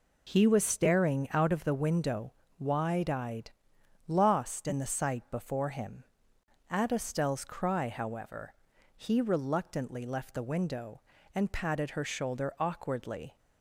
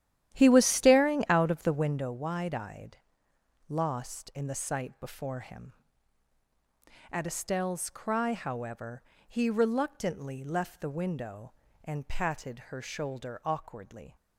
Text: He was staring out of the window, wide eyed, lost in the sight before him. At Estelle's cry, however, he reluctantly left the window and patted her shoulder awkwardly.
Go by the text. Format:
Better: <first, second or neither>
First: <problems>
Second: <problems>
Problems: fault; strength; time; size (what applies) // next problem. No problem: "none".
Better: first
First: none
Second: starts louder than the rest; strong; until 2.1 s; 11.5 dB